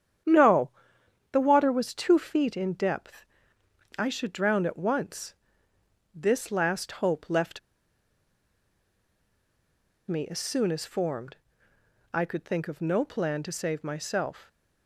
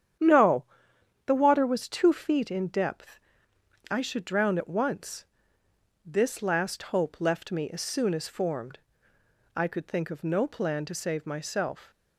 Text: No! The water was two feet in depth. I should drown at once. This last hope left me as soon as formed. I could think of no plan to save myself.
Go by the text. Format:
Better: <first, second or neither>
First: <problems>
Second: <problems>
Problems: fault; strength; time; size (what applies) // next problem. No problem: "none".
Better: second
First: starts louder than the rest; strong; until 1.8 s; 9.5 dB // pauses between "left" and "me"; strong; at 7.5 s; 2.5 s long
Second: starts louder than the rest; strong; until 1.8 s; 9.5 dB